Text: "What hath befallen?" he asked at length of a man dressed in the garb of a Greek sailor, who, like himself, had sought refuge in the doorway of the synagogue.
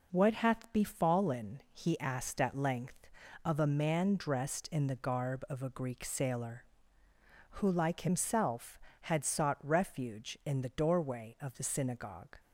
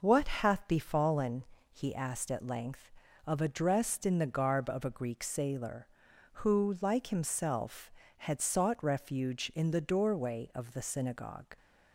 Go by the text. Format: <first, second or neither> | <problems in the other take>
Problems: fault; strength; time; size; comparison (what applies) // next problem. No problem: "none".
first | skips "man"; at 3.4 s